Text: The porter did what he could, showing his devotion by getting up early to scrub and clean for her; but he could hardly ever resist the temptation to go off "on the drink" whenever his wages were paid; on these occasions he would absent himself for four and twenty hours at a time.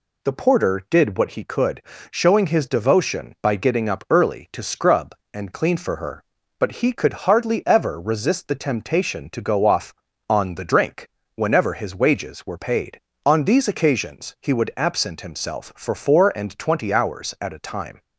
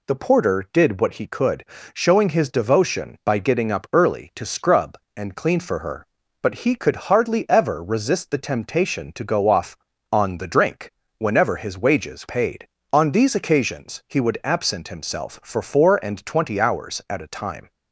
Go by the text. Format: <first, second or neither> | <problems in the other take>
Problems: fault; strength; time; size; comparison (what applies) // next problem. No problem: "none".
first | pauses between "drink" and "whenever"; slight; at 10.9 s; 0.24 s long; slight in the first // skips "were"; at 12.2 s